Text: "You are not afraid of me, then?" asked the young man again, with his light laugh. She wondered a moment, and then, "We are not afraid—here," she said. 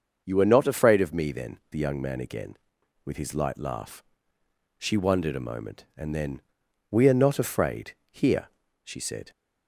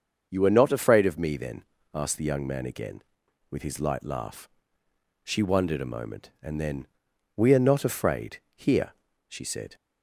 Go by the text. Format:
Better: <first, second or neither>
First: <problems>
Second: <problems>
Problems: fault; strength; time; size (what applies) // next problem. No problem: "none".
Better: second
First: starts louder than the rest; until 1.2 s; 6.5 dB // skips "asked"; at 1.6 s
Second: starts louder than the rest; until 1.3 s; 6.5 dB